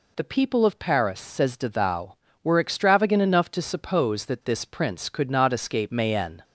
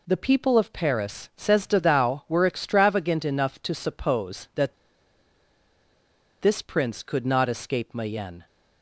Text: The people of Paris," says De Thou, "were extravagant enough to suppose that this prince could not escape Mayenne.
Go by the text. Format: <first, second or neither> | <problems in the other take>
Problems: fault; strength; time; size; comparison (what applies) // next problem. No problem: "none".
first | pauses between "that" and "this"; strong; at 4.7 s; 1.6 s long